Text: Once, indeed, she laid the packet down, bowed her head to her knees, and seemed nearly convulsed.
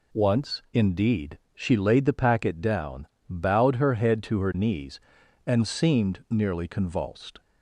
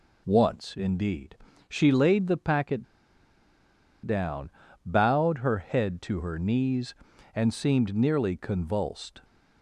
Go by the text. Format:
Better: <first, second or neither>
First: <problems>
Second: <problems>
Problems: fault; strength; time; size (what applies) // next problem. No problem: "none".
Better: first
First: none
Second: pauses between "packet" and "down"; at 2.8 s; 1.2 s long